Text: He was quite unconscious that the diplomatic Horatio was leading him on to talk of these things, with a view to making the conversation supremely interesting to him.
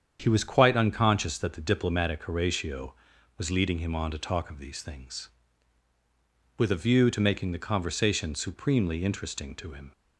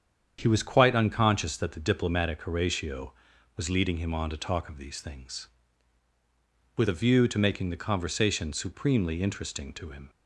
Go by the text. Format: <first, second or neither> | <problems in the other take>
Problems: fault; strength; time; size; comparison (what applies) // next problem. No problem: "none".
neither | starts louder than the rest; strong; the same in both